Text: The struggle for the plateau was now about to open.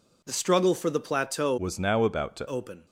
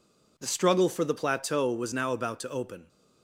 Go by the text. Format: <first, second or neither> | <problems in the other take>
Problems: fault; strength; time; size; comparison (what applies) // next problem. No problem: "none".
second | changes voice from "was" to "to"; from 1.5 to 2.4 s; 0.9 s long